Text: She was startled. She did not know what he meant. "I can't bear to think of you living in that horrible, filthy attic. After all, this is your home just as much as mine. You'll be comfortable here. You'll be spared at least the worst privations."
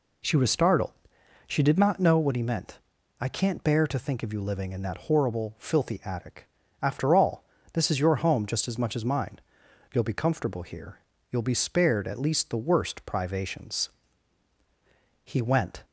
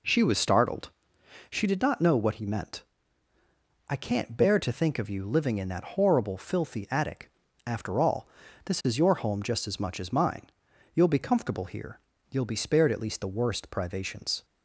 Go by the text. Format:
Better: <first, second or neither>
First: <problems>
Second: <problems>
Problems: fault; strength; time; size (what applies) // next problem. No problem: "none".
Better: second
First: goes on to say "He went"; from 15.2 s on; 0.58 s long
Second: none